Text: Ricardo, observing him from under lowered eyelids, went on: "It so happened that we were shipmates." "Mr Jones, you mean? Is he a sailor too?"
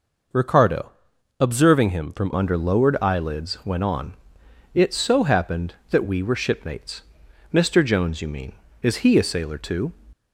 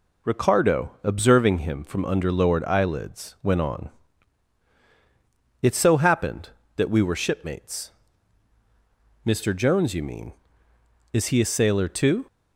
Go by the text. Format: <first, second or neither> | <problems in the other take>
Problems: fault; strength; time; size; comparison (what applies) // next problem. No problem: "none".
second | changes voice at "under"; from 2.3 s on; 7.6 s long